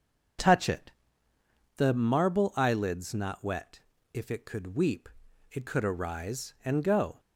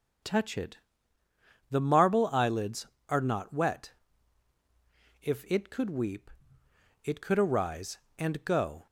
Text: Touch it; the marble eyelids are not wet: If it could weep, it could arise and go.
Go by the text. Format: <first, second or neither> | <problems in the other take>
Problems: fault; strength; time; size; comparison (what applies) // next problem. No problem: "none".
second | starts louder than the rest; until 2.2 s; 6.5 dB; also in the second // skips "are"; at 3.1 s